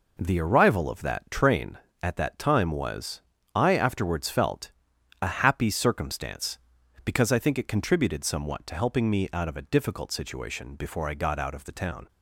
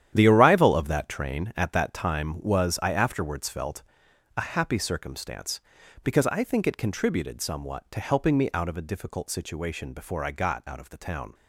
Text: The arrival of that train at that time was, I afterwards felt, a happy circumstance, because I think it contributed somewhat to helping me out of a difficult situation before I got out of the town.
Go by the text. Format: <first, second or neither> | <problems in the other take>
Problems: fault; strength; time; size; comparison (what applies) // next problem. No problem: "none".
first | gets quieter; strong; throughout; 11 dB